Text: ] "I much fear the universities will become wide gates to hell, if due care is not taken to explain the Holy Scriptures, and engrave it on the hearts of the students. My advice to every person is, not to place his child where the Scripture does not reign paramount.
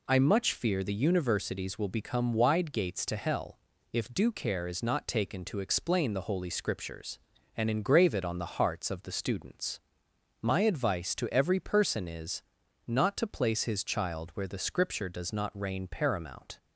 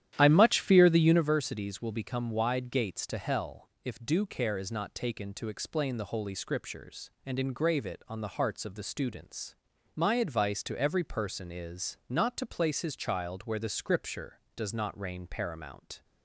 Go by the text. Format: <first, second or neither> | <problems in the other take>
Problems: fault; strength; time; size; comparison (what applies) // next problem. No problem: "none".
first | starts louder than the rest; strong; until 1.4 s; 11 dB